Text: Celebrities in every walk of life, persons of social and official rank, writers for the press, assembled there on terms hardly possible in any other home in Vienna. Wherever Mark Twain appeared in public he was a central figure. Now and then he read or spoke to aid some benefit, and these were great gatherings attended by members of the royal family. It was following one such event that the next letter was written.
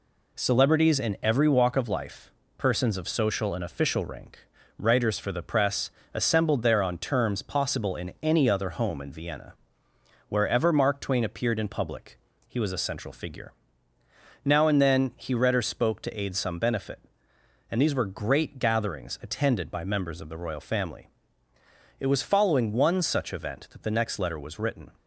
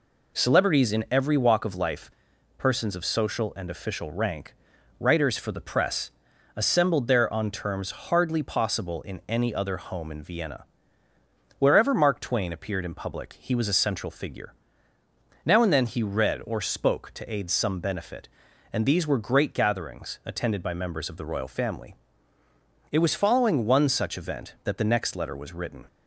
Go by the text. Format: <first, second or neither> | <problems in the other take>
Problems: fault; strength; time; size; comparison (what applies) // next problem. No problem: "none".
second | skips "hardly"; at 7.4 s // pauses between "public" and "he"; slight; at 12.1 s; 0.30 s long